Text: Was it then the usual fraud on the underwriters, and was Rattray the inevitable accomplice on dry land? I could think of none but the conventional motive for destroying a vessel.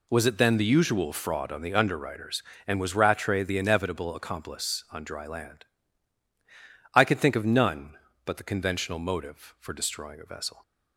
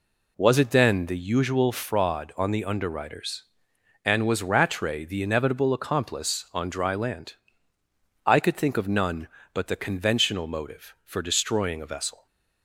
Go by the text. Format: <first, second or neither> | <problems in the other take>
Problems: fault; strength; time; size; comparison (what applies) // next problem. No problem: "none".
neither | none